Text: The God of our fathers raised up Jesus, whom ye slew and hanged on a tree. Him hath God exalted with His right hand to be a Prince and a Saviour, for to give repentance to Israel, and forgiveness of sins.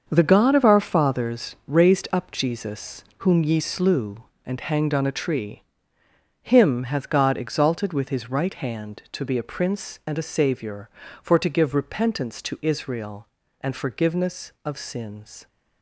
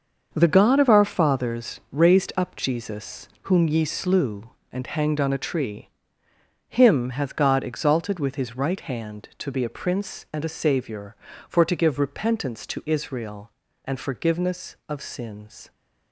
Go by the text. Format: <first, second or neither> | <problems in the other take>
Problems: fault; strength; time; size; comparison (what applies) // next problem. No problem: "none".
neither | starts louder than the rest; the same in both